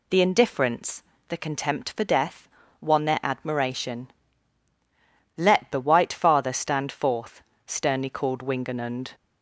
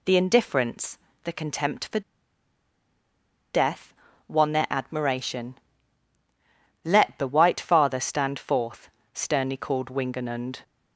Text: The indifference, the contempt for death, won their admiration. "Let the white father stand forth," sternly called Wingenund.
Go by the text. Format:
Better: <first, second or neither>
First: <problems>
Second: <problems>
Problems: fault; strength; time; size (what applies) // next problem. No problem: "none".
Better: first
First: none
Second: pauses between "for" and "death"; strong; at 2.0 s; 1.5 s long